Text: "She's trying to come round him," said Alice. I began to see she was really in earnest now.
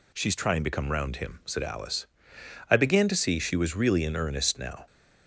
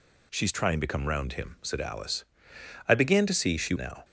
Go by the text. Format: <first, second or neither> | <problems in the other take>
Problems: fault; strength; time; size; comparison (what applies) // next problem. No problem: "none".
first | skips "was really in earnest"; at 3.7 s